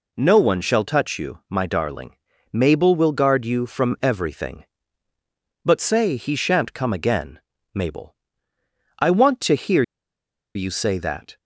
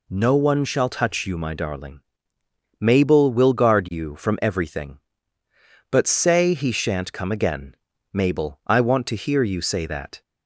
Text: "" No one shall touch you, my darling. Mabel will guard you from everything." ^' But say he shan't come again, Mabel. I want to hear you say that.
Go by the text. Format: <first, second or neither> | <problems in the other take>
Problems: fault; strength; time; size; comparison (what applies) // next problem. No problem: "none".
second | pauses between "hear" and "you"; noticeable; at 9.8 s; 0.73 s long